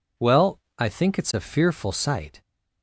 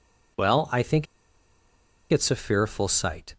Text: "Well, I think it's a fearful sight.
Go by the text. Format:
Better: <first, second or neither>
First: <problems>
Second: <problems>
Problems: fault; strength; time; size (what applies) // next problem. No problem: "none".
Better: first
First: none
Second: pauses between "think" and "it's"; at 1.0 s; 1.0 s long